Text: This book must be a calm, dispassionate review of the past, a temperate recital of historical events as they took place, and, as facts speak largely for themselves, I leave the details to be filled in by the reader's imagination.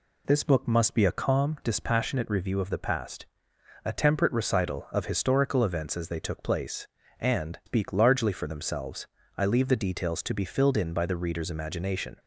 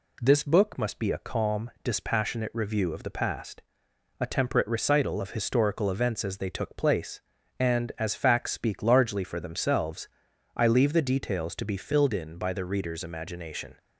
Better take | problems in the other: second | skips "as facts"; at 7.6 s

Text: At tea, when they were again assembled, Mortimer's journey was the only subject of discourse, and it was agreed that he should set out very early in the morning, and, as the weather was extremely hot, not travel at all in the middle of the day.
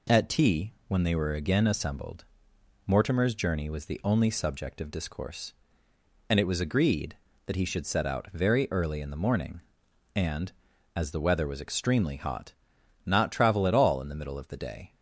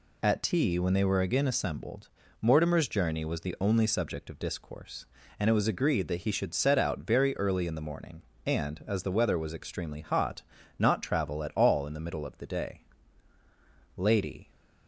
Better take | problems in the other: first | goes on to say "Lady"; from 13.9 s on; 0.54 s long

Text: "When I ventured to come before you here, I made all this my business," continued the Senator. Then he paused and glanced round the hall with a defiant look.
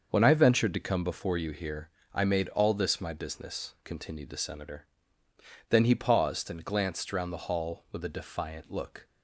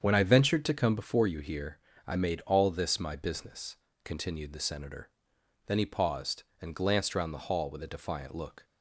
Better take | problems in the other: neither | starts louder than the rest; the same in both

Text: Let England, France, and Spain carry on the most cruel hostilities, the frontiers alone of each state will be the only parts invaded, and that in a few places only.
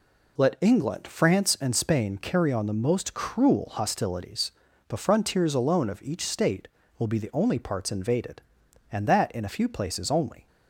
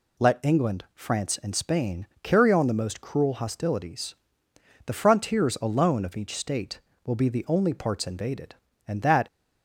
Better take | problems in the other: first | pauses between "Spain" and "carry"; slight; at 2.0 s; 0.16 s long // stops before "in a few places only"; at 9.2 s

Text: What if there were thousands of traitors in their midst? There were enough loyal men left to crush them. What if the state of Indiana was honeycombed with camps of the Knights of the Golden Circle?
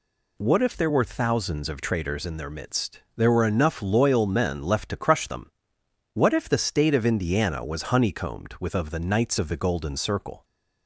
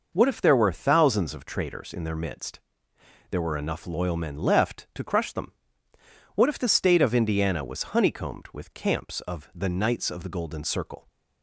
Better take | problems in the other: second | skips "camps"; at 8.7 s

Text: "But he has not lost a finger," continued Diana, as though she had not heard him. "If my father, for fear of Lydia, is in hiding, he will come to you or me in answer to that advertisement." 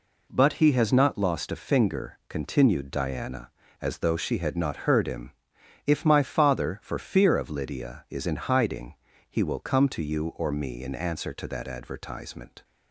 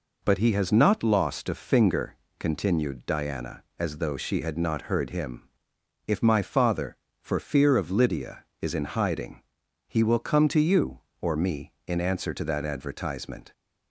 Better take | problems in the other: neither | none

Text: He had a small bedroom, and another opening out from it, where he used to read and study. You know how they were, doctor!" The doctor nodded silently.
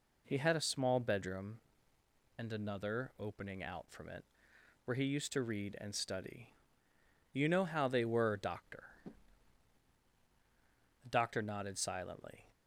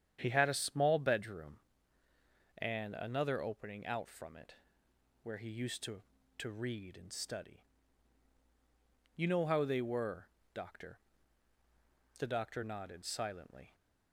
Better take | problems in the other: first | starts louder than the rest; strong; until 1.2 s; 9 dB // says "to" twice; at 6.3 s

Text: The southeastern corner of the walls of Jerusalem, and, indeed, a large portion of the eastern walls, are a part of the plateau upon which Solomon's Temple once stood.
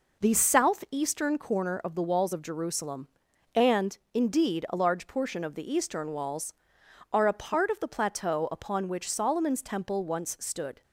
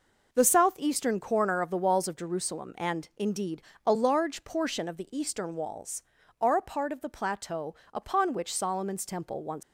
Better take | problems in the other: first | pauses between "plateau" and "upon"; slight; at 7.7 s; 0.18 s long // stops before "stood"; at 9.6 s

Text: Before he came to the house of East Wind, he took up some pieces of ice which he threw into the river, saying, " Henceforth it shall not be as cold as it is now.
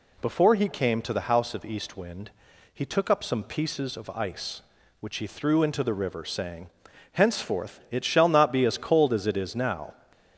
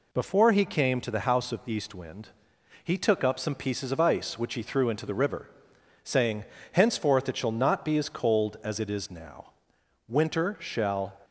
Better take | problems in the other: first | goes on to say "Winter shall"; noticeable; from 10.0 s on; 1.1 s long

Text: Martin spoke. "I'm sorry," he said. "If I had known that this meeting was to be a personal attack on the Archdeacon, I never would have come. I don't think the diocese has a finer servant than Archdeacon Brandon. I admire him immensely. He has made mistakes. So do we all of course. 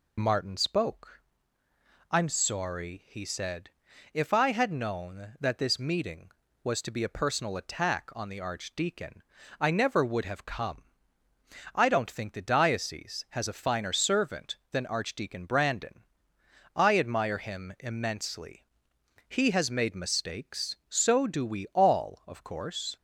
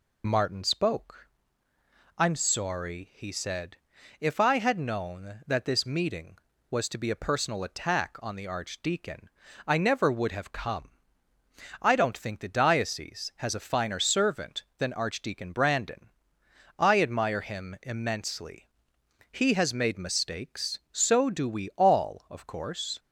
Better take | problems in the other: neither | none

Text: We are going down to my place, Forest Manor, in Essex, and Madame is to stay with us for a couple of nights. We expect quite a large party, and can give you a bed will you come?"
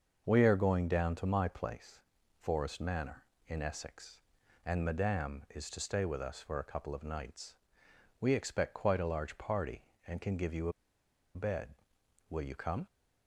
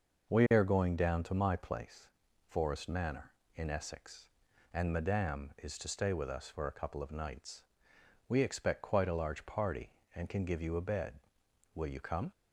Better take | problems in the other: second | starts louder than the rest; until 1.2 s; 6.5 dB; noticeable in the second // pauses between "a" and "bed"; noticeable; at 10.7 s; 0.64 s long

